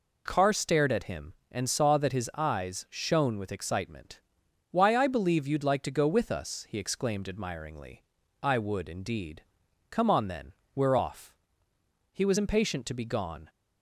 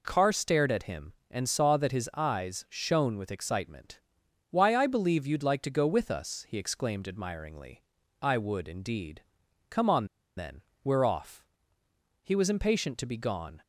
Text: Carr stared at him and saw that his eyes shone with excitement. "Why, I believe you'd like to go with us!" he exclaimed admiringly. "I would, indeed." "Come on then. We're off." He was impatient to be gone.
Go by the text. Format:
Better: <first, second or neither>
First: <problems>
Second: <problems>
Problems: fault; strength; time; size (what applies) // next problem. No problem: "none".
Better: first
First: none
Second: pauses between "on" and "then"; slight; at 10.0 s; 0.31 s long